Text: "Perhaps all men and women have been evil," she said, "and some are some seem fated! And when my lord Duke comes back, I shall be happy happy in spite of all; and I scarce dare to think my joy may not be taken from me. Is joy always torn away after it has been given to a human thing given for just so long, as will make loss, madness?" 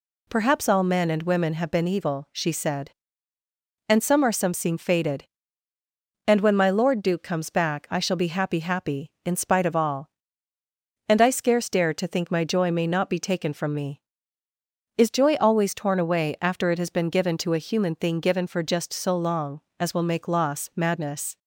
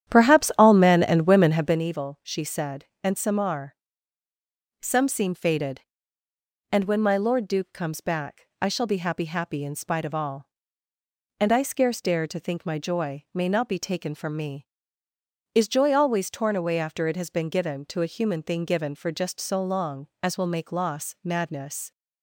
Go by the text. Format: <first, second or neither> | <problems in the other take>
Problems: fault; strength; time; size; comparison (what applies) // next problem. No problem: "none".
first | starts louder than the rest; strong; until 1.8 s; 10.5 dB // pauses between "are" and "some"; at 3.7 s; 1.0 s long